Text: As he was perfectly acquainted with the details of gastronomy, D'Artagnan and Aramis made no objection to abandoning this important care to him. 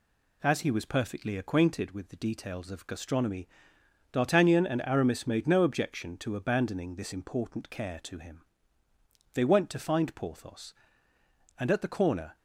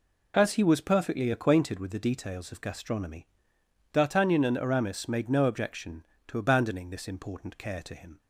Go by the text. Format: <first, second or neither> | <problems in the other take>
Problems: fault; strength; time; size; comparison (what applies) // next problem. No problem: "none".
second | goes on to say "They went to find Porthos and at the corner"; strong; from 9.3 s on; 3.0 s long